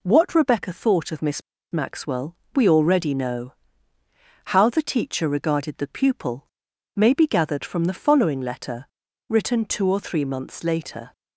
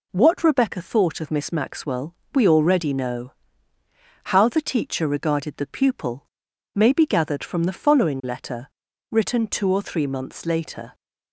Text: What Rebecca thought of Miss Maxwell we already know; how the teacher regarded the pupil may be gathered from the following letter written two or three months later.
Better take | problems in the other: second | pauses between "Miss" and "Maxwell"; slight; at 1.4 s; 0.30 s long // pauses between "Maxwell" and "we"; slight; at 2.3 s; 0.18 s long; slight in the second // pauses between "pupil" and "may"; noticeable; at 6.4 s; 0.50 s long; noticeable in the second // pauses between "letter" and "written"; at 8.8 s; 0.44 s long; also in the second

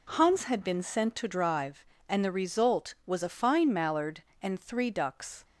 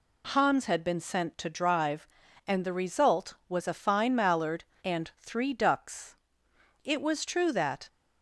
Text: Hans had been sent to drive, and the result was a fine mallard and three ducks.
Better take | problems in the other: first | goes on to say "It was true that"; noticeable; from 6.8 s on; 1.0 s long

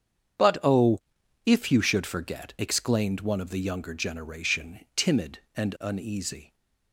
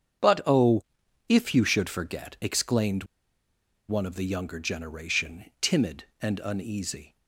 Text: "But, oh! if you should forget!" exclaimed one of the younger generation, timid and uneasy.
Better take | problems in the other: first | starts louder than the rest; strong; until 1.7 s; 8 dB; strong in the first // pauses between "exclaimed" and "one"; noticeable; at 3.0 s; 0.84 s long

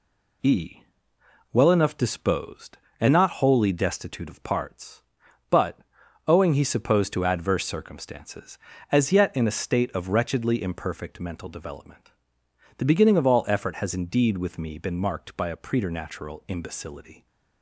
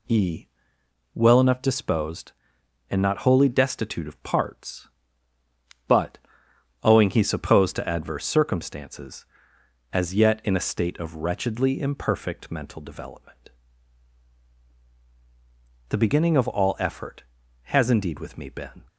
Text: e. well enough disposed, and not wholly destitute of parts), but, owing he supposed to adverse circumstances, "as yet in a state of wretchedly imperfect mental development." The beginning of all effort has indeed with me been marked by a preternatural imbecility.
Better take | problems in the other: first | stops before "marked by a preternatural imbecility"; at 18.8 s

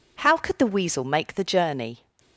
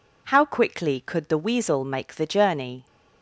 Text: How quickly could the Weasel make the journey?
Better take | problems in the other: second | skips "quickly"; at 0.3 s

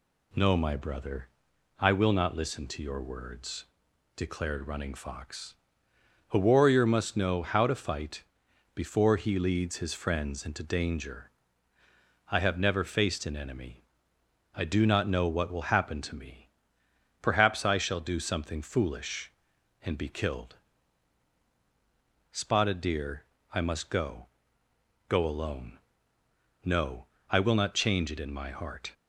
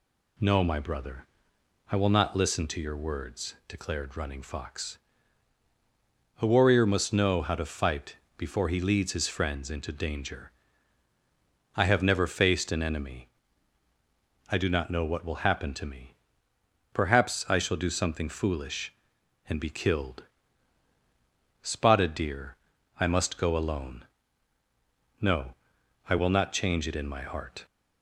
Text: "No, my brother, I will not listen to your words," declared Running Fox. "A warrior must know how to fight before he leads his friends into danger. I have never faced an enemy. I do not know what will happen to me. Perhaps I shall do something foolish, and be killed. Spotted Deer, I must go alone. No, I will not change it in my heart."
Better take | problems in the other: second | pauses between "fight" and "before"; noticeable; at 8.2 s; 0.50 s long; slight in the second // says "go" twice; at 25.0 s

